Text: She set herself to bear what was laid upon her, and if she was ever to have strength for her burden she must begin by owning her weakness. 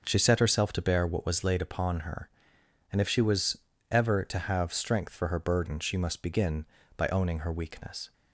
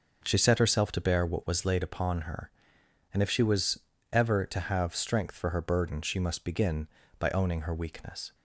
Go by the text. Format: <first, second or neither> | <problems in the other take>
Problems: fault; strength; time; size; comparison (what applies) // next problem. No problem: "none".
neither | starts louder than the rest; the same in both // pauses between "was" and "ever"; slight; the same in both